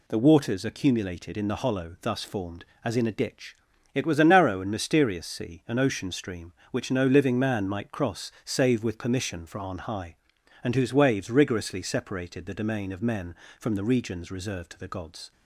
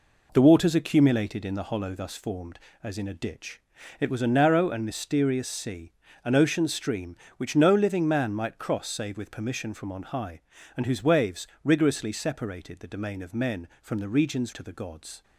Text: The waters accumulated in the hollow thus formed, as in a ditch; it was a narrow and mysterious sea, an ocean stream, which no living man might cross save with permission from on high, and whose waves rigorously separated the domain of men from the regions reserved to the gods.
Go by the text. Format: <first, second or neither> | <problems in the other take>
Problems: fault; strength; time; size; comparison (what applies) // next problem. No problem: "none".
first | pauses between "waves" and "rigorously"; slight; at 11.4 s; 0.16 s long // skips "reserved"; at 14.5 s